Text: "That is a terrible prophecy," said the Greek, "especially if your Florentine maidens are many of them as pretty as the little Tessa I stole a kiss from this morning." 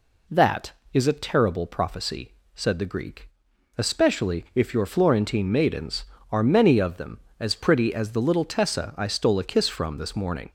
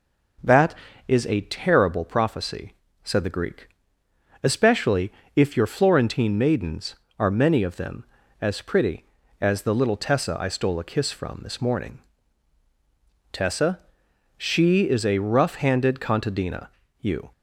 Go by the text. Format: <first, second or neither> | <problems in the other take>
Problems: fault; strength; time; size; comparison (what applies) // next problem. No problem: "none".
first | pauses between "especially" and "if"; slight; at 5.1 s; 0.24 s long // goes on to say "Tessa she is a rough handed contadina you"; strong; from 13.3 s on; 3.9 s long